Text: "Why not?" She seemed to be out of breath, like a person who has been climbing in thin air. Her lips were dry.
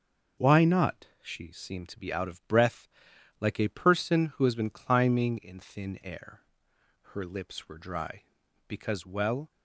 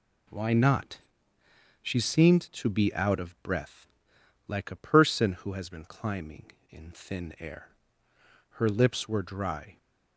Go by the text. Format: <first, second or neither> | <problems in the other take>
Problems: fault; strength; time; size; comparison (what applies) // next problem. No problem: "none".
second | starts louder than the rest; noticeable; until 1.5 s; 6 dB // goes on to say "Because well"; noticeable; from 8.6 s on; 0.82 s long